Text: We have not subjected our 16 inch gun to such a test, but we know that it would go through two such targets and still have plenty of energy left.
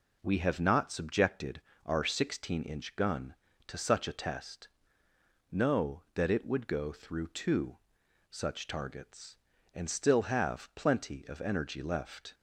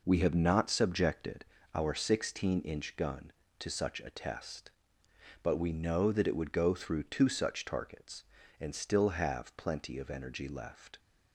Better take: second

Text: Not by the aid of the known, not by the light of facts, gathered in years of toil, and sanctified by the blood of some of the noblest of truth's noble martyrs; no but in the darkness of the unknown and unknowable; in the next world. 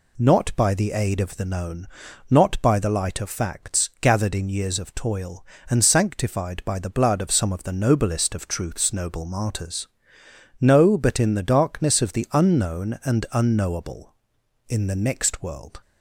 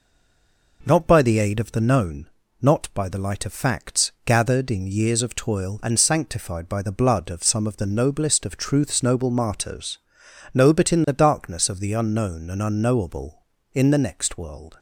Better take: first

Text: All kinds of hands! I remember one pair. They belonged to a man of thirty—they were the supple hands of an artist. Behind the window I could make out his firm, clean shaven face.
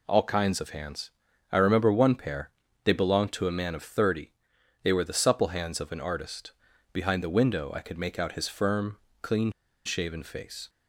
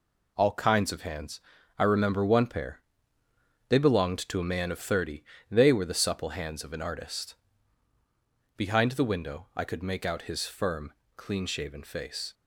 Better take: second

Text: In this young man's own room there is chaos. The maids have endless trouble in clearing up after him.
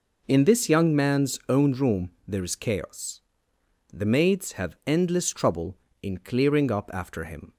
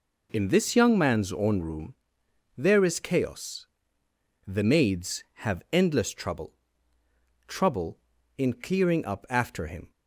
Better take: first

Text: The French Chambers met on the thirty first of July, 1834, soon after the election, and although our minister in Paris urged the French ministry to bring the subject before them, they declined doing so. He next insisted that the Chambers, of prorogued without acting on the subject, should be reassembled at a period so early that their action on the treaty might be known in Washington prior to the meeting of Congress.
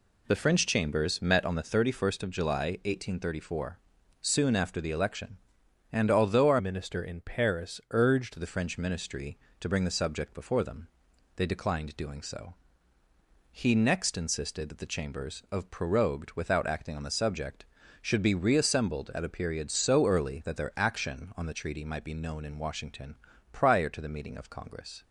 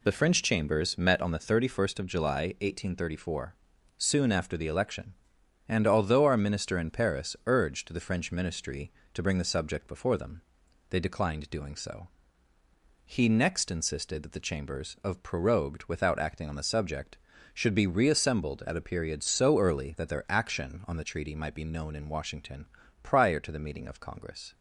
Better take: second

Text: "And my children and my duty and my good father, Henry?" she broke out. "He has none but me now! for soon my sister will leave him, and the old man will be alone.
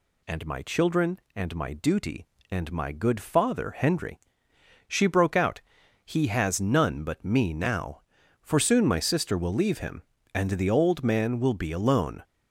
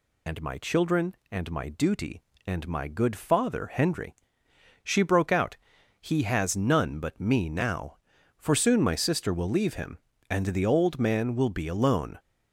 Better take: first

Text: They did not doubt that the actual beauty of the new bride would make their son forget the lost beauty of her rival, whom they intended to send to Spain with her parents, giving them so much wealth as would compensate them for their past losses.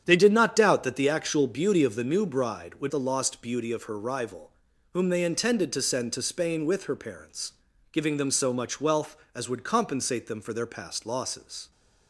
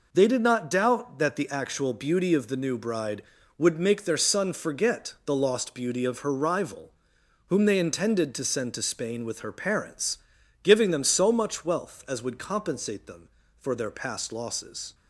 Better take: second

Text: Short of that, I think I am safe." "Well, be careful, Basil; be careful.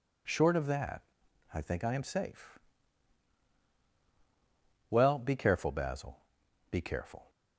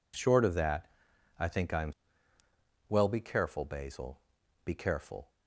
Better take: first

